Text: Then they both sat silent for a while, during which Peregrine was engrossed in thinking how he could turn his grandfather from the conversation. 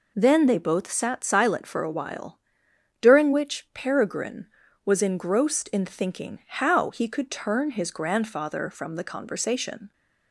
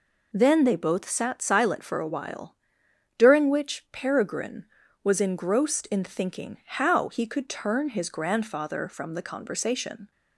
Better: neither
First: none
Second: none

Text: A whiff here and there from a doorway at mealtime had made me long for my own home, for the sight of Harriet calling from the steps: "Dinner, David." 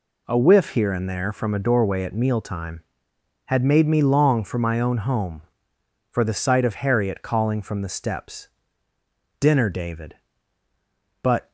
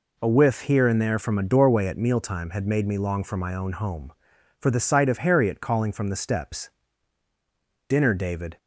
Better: second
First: goes on to say "But"; slight; from 11.2 s on; 0.30 s long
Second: none

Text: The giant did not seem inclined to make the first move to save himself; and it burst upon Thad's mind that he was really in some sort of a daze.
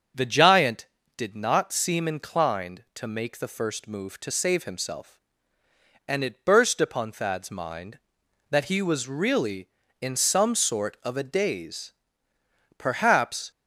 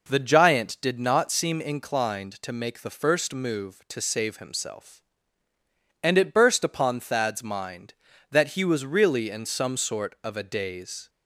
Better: second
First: starts louder than the rest; until 1.4 s; 7 dB // goes on to say "Perhaps"; noticeable; from 12.7 s on; 0.72 s long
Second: none

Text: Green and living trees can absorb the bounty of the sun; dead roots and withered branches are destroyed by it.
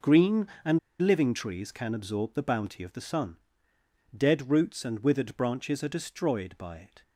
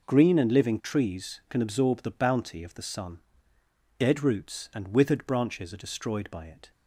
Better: second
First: pauses between "and" and "living"; slight; at 0.7 s; 0.22 s long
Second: none

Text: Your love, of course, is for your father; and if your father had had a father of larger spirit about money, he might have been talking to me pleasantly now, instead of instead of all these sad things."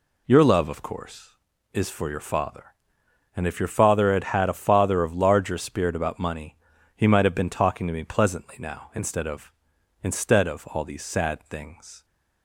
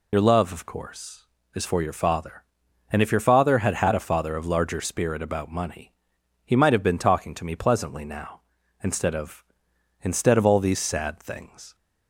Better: first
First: none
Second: loses the start of "Your"; at 0.1 s; 60 ms

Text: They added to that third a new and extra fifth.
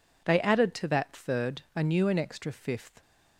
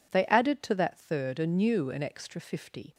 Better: first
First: none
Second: says "fifty" for "fifth"; at 2.4 s

